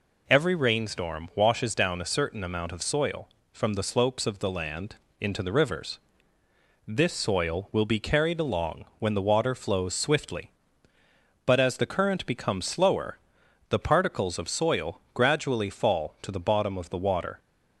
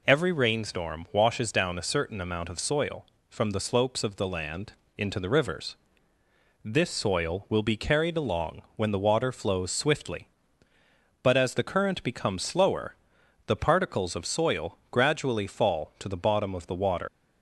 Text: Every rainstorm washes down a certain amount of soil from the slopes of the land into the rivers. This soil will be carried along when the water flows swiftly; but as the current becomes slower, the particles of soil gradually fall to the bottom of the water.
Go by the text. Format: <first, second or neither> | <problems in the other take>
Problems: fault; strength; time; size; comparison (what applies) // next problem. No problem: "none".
first | pauses between "land" and "into"; slight; at 4.7 s; 0.24 s long; slight in the first // leaves "water" unfinished; at 17.0 s; 80 ms